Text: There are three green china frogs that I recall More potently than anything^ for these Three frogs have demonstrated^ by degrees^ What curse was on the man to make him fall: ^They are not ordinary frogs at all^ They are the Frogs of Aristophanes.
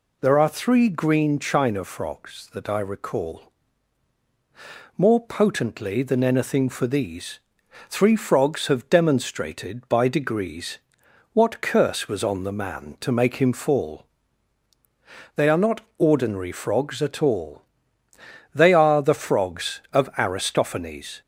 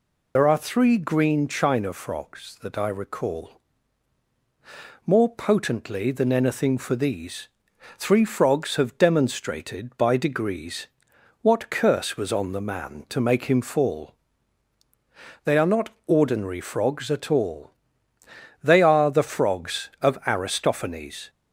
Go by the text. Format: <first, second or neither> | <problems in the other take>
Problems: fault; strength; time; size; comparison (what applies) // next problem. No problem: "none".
first | loses the start of "There"; at 0.3 s; 55 ms // pauses between "recall" and "More"; strong; at 3.5 s; 1.4 s long; strong in the first // pauses between "these" and "Three"; noticeable; at 7.4 s; 0.50 s long; noticeable in the first // pauses between "degrees" and "What"; noticeable; at 10.8 s; 0.54 s long; noticeable in the first // pauses between "not" and "ordinary"; slight; at 15.8 s; 0.18 s long; slight in the first // pauses between "all" and "They"; noticeable; at 17.6 s; 0.94 s long; noticeable in the first